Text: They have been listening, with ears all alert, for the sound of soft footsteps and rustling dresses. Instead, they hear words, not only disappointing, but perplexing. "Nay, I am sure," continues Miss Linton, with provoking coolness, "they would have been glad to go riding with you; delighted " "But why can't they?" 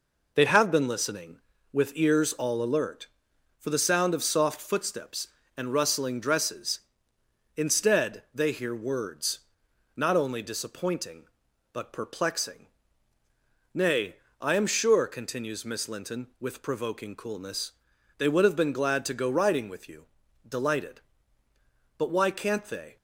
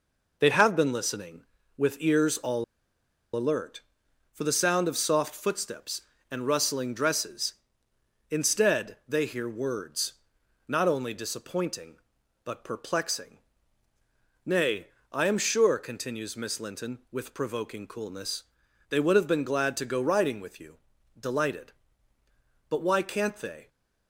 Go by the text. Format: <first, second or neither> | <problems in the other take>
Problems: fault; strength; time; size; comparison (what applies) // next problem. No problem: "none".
first | pauses between "all" and "alert"; noticeable; at 2.6 s; 0.71 s long